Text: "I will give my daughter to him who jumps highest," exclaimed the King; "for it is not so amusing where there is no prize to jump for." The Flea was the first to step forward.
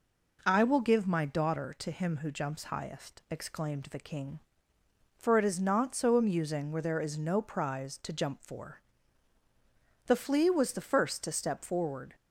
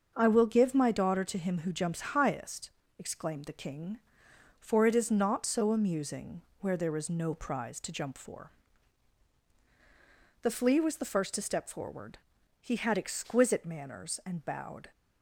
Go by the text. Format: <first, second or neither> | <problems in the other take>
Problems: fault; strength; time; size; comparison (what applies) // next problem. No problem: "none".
first | starts louder than the rest; until 1.1 s; 6.5 dB // pauses between "amusing" and "where"; slight; at 6.4 s; 0.16 s long // goes on to say "He had exquisite manners and bowed"; strong; from 12.6 s on; 2.3 s long